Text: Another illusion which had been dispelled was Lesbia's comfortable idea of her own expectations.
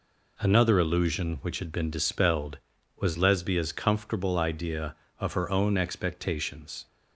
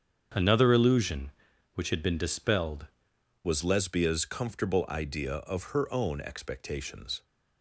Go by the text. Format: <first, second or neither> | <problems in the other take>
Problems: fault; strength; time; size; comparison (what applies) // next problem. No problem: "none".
first | starts louder than the rest; strong; until 1.7 s; 7.5 dB // changes voice at "was"; from 3.4 s on; 3.8 s long